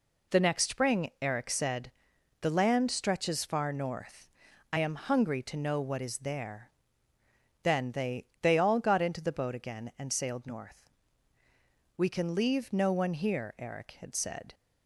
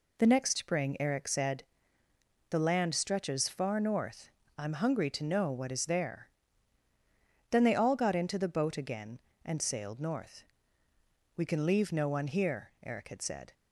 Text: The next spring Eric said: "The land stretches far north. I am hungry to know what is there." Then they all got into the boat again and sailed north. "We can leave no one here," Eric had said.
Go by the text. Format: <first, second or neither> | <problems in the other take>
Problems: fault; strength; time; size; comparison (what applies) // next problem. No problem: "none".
second | says "they" twice; at 8.3 s